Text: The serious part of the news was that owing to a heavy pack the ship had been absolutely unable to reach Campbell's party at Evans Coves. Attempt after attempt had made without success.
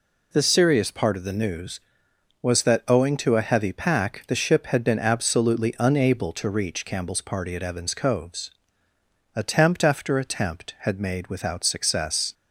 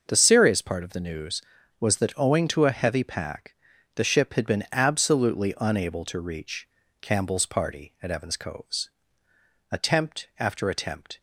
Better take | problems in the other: first | starts louder than the rest; until 1.0 s; 6.5 dB // pauses between "pack" and "the"; at 3.5 s; 0.40 s long // pauses between "reach" and "Campbell's"; slight; at 6.6 s; 0.34 s long // stops before "had made without success"; at 11.1 s

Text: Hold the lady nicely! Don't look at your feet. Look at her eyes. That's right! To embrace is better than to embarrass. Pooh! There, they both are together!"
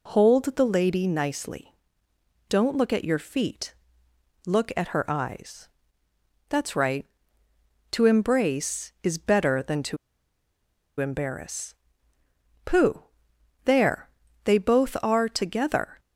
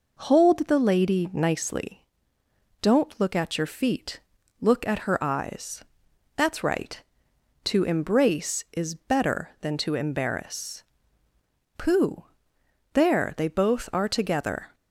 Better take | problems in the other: second | pauses between "to" and "embarrass"; at 9.9 s; 1.0 s long

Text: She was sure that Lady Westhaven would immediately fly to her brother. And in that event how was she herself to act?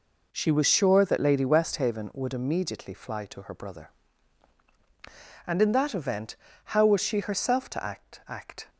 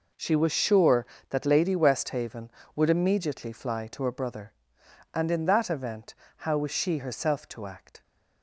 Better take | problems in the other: second | pauses between "event" and "how"; slight; at 6.3 s; 0.36 s long; slight in the second // says "act" twice; at 8.2 s

